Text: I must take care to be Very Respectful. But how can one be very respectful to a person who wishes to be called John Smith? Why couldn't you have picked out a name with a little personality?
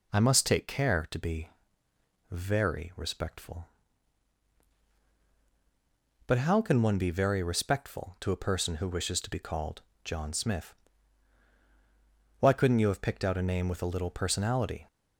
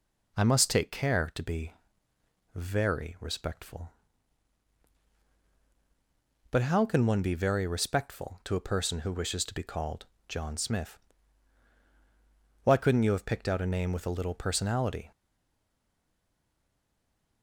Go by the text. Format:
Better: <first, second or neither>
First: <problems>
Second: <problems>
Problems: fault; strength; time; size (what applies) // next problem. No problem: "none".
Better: first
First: pauses between "be" and "Very"; noticeable; at 1.4 s; 0.82 s long // pauses between "called" and "John"; slight; at 9.8 s; 0.24 s long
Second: pauses between "be" and "Very"; noticeable; at 1.7 s; 0.82 s long // pauses between "called" and "John"; slight; at 10.0 s; 0.24 s long // stays silent after the last word; from 15.1 s on; 2.3 s long